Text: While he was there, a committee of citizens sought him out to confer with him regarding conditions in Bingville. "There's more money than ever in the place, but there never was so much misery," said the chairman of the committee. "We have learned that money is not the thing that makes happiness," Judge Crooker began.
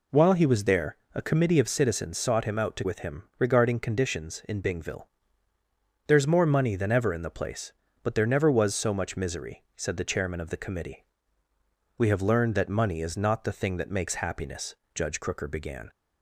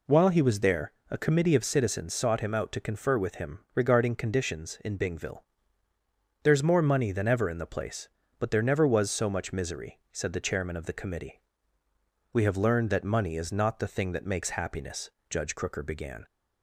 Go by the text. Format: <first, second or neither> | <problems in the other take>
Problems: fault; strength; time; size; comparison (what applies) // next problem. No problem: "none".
second | skips "confer"; at 2.8 s // pauses between "him" and "regarding"; slight; at 3.2 s; 0.16 s long; slight in the second